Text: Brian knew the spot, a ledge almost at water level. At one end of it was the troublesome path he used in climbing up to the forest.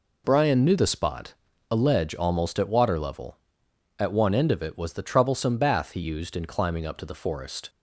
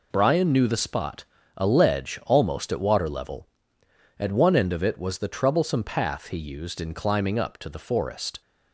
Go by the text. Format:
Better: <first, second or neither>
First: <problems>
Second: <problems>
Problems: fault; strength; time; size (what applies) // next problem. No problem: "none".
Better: second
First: says "bath" for "path"; at 5.5 s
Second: none